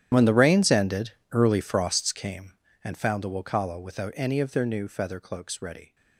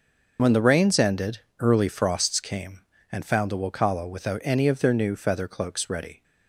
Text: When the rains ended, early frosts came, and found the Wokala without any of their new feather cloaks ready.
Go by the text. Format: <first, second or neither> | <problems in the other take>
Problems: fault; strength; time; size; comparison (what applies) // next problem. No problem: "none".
second | gets quieter; strong; throughout; 19.5 dB // starts louder than the rest; strong; until 1.1 s; 11 dB; also in the second